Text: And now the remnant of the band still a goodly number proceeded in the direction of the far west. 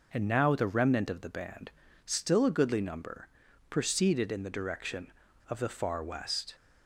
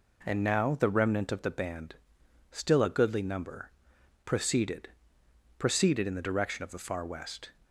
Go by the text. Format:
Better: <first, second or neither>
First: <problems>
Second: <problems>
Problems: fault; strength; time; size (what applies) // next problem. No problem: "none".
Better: first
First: pauses between "band" and "still"; slight; at 1.7 s; 0.34 s long // pauses between "number" and "proceeded"; at 3.2 s; 0.40 s long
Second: pauses between "band" and "still"; noticeable; at 1.9 s; 0.56 s long // pauses between "number" and "proceeded"; noticeable; at 3.7 s; 0.54 s long // says "proceeded" twice; at 5.5 s